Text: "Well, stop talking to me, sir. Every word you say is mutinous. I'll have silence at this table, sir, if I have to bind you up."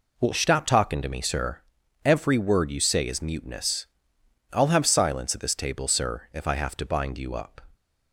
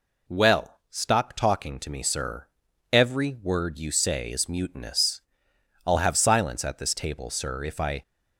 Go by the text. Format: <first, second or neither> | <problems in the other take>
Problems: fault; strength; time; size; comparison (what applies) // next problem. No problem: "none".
first | stops before "have to bind you up"; at 8.0 s